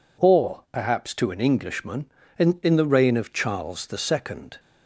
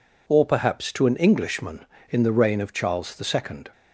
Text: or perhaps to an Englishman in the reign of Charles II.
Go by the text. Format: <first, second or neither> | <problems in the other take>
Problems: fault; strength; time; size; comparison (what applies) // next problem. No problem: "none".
second | says "in" twice; at 2.6 s